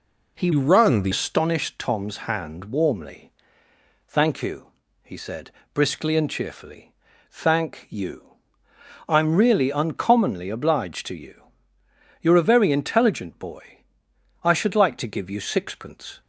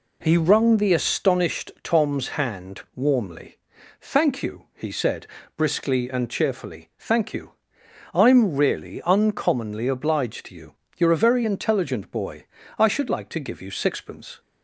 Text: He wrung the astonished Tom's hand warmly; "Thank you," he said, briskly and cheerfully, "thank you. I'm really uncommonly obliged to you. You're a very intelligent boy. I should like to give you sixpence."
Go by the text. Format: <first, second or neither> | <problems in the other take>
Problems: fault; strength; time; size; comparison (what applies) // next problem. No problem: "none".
second | changes voice from "wrung" to "the"; from 0.5 to 1.1 s; 0.6 s long